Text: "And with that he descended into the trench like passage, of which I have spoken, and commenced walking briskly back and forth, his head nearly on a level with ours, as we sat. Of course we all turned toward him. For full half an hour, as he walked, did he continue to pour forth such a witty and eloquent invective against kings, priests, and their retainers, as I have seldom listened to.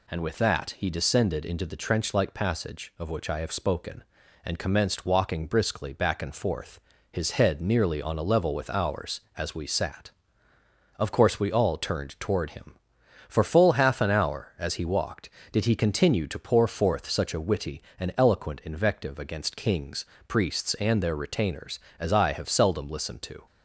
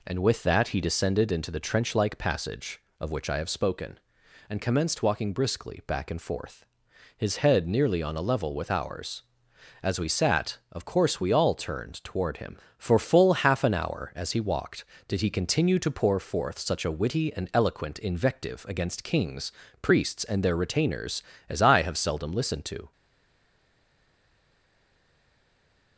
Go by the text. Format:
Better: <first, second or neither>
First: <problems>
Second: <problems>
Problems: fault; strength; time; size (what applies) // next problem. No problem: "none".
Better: first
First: none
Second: stays silent after the last word; strong; from 22.9 s on; 3.0 s long